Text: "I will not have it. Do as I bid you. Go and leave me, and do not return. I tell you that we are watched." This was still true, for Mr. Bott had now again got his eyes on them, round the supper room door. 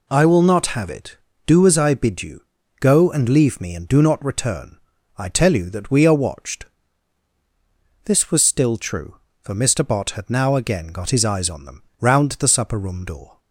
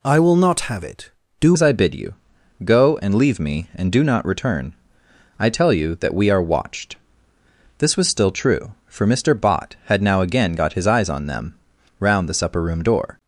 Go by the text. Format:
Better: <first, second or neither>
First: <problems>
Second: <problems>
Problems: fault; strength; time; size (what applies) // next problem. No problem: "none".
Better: first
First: none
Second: changes voice at "as"; from 1.5 s on; 11.6 s long